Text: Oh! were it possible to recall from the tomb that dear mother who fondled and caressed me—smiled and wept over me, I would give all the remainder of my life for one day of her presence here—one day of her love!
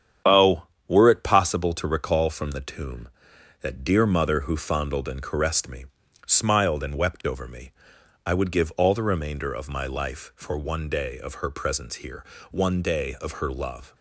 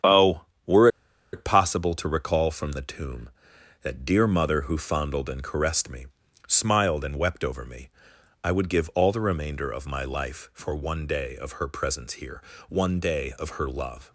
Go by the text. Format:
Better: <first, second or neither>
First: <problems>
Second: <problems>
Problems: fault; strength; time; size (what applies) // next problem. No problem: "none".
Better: first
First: starts louder than the rest; strong; until 1.4 s; 8.5 dB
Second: starts louder than the rest; strong; until 1.7 s; 8.5 dB // pauses between "were" and "it"; at 0.8 s; 0.45 s long